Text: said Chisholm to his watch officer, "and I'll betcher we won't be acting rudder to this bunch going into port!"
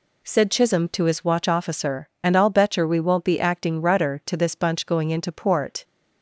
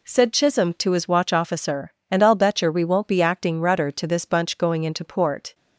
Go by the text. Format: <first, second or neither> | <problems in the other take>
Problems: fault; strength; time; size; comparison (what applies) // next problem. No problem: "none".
neither | none